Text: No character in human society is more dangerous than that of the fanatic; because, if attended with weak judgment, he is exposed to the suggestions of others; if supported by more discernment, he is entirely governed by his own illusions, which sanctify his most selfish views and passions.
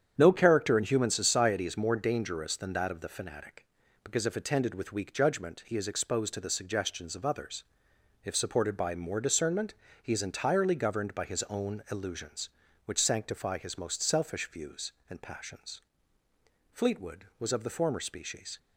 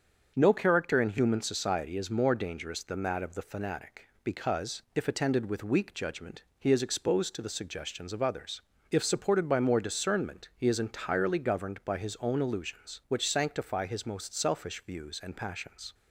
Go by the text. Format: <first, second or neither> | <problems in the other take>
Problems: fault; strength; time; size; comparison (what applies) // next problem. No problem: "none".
second | starts louder than the rest; strong; until 1.1 s; 8.5 dB; also in the second // goes on to say "Fleetwood was of the former species"; strong; from 16.7 s on; 1.8 s long